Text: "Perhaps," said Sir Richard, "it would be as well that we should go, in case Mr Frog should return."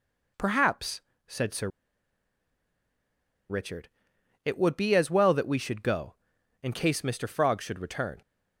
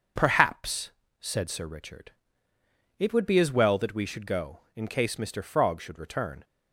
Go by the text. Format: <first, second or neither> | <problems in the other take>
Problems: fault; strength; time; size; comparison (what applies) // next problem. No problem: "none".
second | pauses between "Sir" and "Richard"; strong; at 1.6 s; 1.8 s long